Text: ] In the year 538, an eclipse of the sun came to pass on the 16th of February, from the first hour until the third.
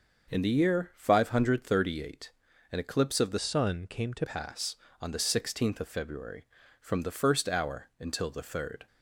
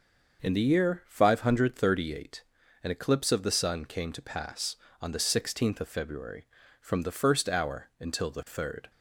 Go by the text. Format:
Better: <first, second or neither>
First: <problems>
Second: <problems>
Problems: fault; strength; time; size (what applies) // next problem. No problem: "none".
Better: second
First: starts louder than the rest; until 1.3 s; 6 dB // changes voice from "sun" to "to"; from 3.3 to 4.2 s; 0.9 s long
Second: starts louder than the rest; noticeable; until 1.4 s; 6 dB